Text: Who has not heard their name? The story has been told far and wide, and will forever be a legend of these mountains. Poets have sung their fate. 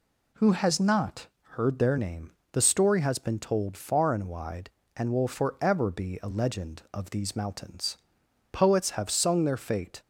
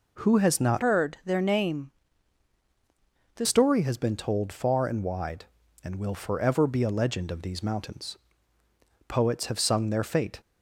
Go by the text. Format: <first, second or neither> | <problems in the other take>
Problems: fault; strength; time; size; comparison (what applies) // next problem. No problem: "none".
first | changes voice from "heard" to "The"; from 0.8 to 3.4 s; 2.6 s long